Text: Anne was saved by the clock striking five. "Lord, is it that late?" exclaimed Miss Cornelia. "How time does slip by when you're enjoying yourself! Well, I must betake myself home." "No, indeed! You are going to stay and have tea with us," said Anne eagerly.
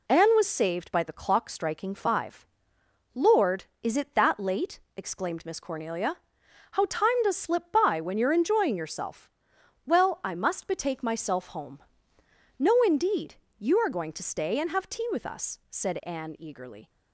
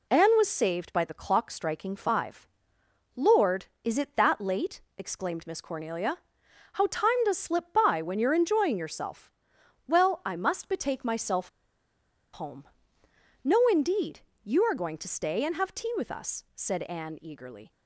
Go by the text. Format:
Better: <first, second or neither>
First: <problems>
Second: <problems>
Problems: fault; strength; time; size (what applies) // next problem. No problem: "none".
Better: first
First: none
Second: pauses between "myself" and "home"; noticeable; at 11.4 s; 0.84 s long